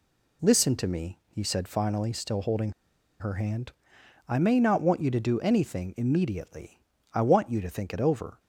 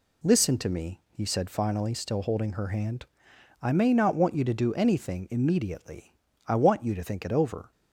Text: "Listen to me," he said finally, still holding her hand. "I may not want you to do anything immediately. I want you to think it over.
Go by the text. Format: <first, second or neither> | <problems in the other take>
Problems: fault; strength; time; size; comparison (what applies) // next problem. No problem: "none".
second | pauses between "holding" and "her"; noticeable; at 2.7 s; 0.49 s long